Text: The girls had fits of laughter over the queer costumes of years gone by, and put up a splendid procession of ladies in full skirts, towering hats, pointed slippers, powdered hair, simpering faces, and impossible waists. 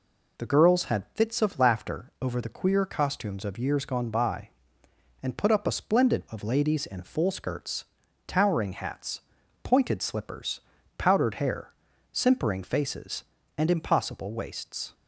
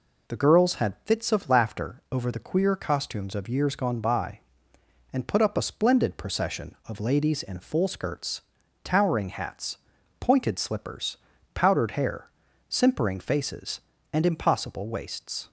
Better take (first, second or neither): second